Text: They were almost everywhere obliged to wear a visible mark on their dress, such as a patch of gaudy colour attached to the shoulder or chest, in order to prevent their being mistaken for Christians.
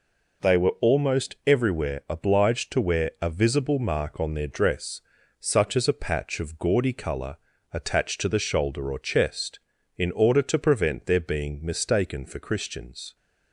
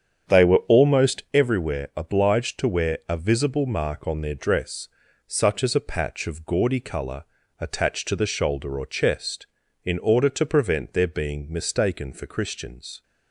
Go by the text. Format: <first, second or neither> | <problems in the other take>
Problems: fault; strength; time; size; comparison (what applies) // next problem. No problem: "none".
first | starts louder than the rest; strong; until 1.3 s; 8 dB // pauses between "colour" and "attached"; slight; at 7.2 s; 0.34 s long; slight in the first